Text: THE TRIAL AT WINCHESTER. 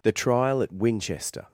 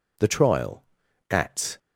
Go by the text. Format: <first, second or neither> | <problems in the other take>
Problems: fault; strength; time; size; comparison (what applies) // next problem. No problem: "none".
first | stops before "WINCHESTER"; at 1.7 s